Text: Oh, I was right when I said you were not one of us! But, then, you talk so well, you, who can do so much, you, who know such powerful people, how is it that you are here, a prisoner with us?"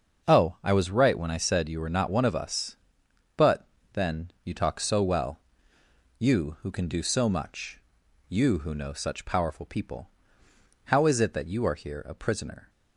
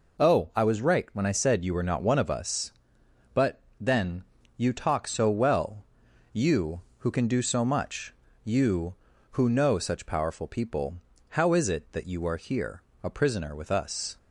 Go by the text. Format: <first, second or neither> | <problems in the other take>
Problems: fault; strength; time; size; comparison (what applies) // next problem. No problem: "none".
second | starts louder than the rest; until 1.3 s; 6.5 dB // stops before "with us"; at 12.6 s